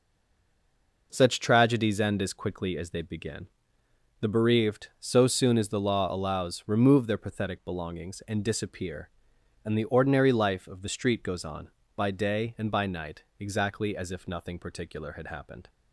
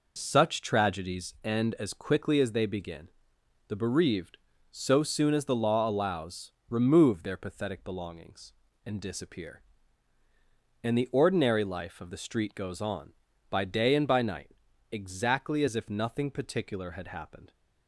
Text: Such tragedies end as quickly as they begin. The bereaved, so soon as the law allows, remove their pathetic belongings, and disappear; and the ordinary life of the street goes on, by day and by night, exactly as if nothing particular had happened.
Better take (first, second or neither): second